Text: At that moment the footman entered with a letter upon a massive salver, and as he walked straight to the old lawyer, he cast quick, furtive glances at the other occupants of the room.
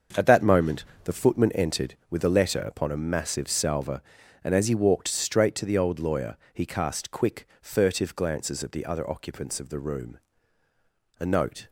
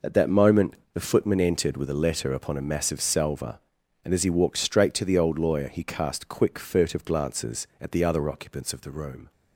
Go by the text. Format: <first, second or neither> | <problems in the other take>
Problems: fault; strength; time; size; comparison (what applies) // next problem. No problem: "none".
second | starts louder than the rest; until 1.3 s; 6.5 dB // pauses between "moment" and "the"; slight; at 0.8 s; 0.22 s long; slight in the second // goes on to say "A note"; from 11.1 s on; 0.52 s long